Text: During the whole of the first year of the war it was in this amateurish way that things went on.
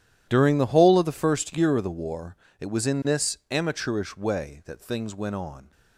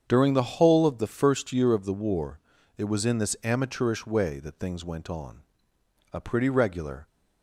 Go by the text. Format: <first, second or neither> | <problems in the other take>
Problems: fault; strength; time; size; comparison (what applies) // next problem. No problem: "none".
first | starts louder than the rest; strong; until 1.0 s; 8 dB // pauses between "war" and "it"; at 2.3 s; 0.38 s long; slight in the first // goes on to say "A pretty regular"; noticeable; from 6.1 s on; 0.94 s long